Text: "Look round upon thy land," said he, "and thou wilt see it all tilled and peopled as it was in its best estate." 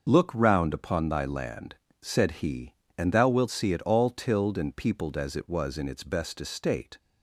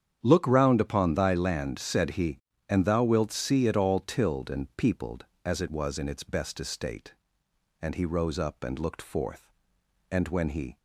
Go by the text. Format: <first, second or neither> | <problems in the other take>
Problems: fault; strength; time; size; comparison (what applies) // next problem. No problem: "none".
first | starts louder than the rest; strong; until 1.2 s; 8.5 dB; noticeable in the first // goes on to say "And he rose up and looked forth And when he"; strong; from 7.8 s on; 2.9 s long